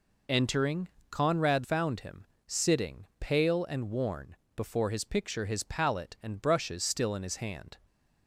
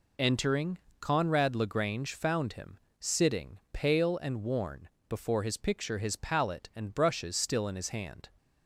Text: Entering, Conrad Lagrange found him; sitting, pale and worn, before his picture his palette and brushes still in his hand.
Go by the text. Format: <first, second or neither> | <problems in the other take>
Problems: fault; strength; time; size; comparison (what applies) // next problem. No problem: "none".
second | skips "Lagrange"; at 1.6 s